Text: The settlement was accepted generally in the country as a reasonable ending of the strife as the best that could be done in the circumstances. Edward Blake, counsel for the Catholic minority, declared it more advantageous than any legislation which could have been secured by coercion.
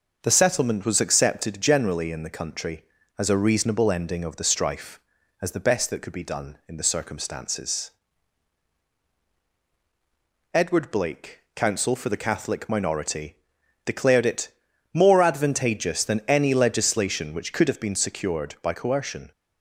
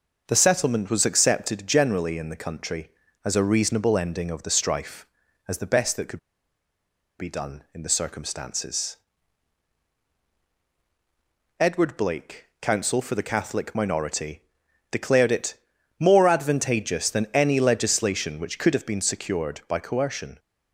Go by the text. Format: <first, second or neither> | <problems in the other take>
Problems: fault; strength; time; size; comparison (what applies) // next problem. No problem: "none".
first | pauses between "could" and "be"; at 6.1 s; 0.99 s long // pauses between "it" and "more"; noticeable; at 15.5 s; 0.46 s long; noticeable in the first